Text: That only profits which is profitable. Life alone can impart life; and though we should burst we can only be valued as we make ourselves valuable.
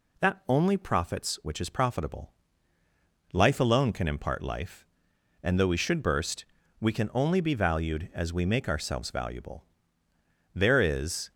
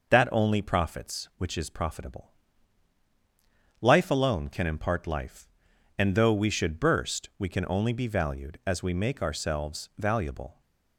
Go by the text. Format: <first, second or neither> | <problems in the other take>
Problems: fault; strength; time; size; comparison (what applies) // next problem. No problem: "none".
second | pauses between "burst" and "we"; slight; at 6.4 s; 0.34 s long // goes on to say "There is"; noticeable; from 10.5 s on; 0.78 s long